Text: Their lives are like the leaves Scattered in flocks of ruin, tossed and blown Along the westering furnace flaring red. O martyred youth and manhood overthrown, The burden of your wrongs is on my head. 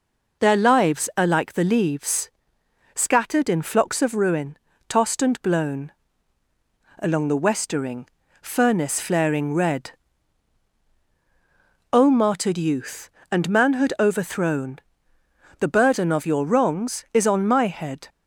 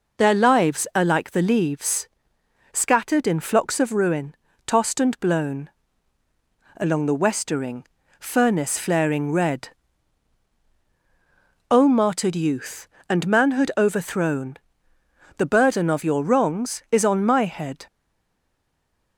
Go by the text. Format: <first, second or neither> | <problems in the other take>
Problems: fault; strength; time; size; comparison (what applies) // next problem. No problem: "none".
first | pauses between "leaves" and "Scattered"; noticeable; at 2.0 s; 0.68 s long; noticeable in the first // pauses between "blown" and "Along"; at 5.7 s; 1.0 s long; also in the first // pauses between "westering" and "furnace"; slight; at 7.8 s; 0.34 s long; slight in the first // stays silent after the last word; noticeable; from 17.8 s on; 1.3 s long